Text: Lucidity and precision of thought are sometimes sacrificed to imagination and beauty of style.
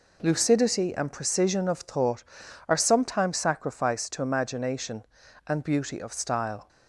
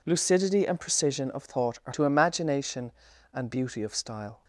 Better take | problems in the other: first | skips "sometimes sacrificed"; at 1.9 s

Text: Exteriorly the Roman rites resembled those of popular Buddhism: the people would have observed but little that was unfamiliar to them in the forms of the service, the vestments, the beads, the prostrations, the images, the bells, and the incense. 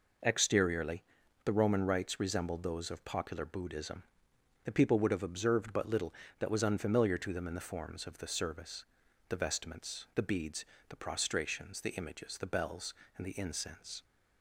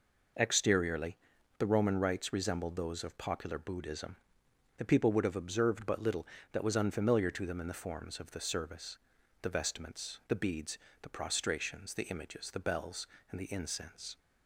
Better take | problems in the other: neither | pauses between "Exteriorly" and "the"; the same in both

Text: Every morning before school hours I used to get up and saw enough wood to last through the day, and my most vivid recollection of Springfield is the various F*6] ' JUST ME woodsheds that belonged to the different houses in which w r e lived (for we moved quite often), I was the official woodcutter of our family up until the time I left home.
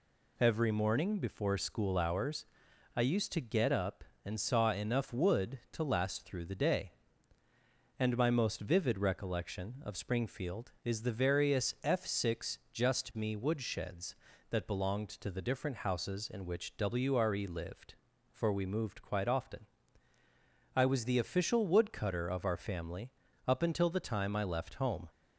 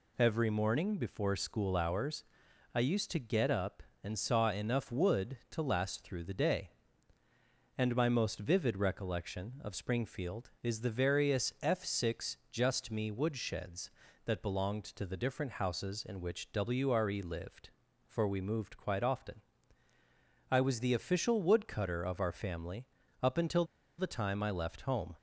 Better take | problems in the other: first | pauses between "hours" and "I"; noticeable; at 2.2 s; 0.50 s long; noticeable in the first // pauses between "family" and "up"; slight; at 22.8 s; 0.34 s long; slight in the first // pauses between "until" and "the"; slight; at 23.6 s; 0.34 s long

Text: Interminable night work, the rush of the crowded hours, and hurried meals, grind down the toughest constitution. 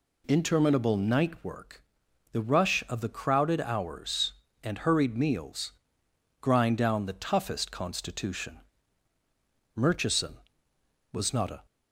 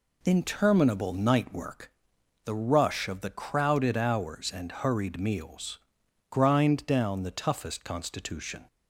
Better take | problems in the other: second | goes on to say "Murchison was not a"; strong; from 9.8 s on; 1.8 s long

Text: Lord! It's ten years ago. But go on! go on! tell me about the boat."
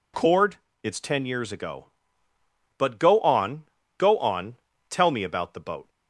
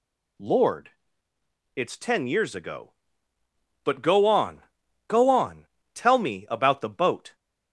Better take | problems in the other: second | says "Cord" for "Lord"; at 0.1 s

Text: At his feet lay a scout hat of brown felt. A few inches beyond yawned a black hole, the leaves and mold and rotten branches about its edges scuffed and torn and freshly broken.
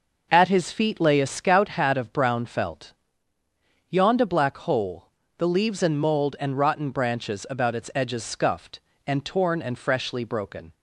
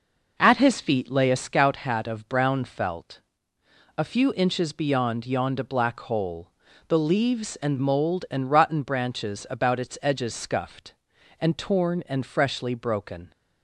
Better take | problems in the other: second | skips "A few inches beyond"; at 3.3 s

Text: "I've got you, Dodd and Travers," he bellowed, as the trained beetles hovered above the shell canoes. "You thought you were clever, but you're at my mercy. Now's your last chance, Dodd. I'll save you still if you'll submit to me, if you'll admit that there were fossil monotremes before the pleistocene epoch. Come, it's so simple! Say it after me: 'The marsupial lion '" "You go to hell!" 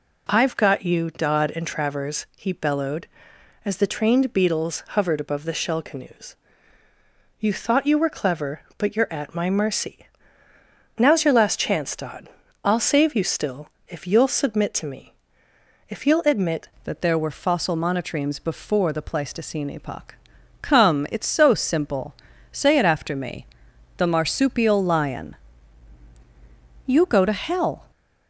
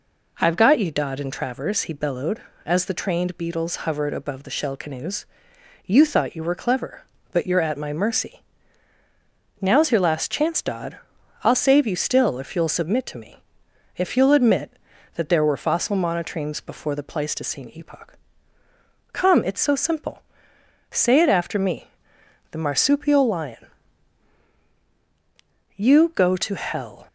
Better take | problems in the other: second | pauses between "still" and "if"; slight; at 13.6 s; 0.18 s long // changes voice at "that"; from 16.8 s on; 11.1 s long

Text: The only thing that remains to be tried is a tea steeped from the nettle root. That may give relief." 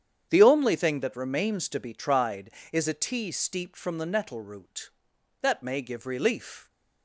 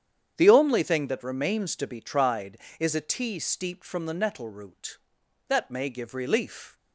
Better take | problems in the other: neither | starts louder than the rest; strong; the same in both

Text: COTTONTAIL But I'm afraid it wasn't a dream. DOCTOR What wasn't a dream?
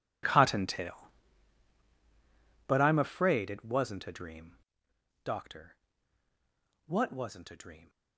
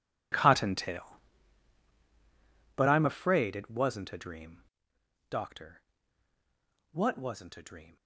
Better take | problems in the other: neither | pauses between "DOCTOR" and "What"; the same in both

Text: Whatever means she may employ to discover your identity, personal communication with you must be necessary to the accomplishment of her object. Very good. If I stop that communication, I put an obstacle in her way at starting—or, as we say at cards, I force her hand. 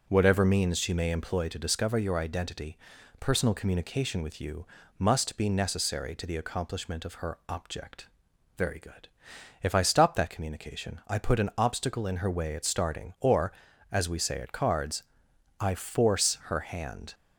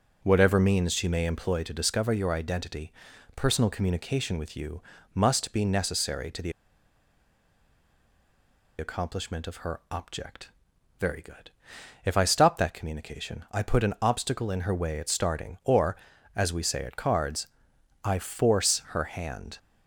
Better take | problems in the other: first | pauses between "you" and "must"; slight; at 4.8 s; 0.32 s long; slight in the first // pauses between "the" and "accomplishment"; strong; at 6.5 s; 2.2 s long

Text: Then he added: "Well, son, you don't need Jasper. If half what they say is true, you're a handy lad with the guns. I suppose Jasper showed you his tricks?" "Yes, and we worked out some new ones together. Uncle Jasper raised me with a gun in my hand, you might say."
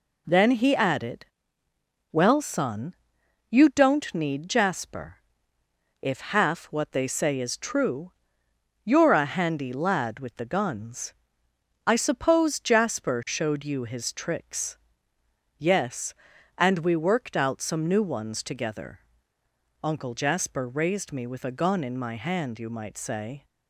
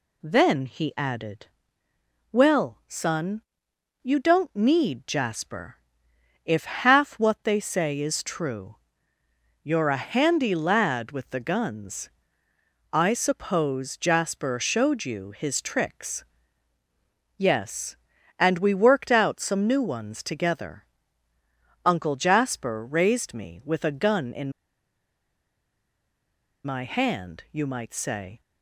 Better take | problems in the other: first | pauses between "in" and "my"; strong; at 24.5 s; 2.1 s long

